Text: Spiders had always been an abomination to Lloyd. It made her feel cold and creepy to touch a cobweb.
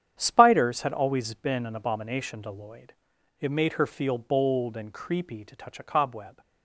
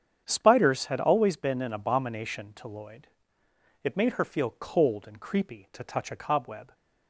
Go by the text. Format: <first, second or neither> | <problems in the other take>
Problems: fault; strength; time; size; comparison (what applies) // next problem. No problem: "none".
second | starts louder than the rest; strong; until 1.1 s; 9 dB; strong in the second // says "bold" for "cold"; at 4.1 s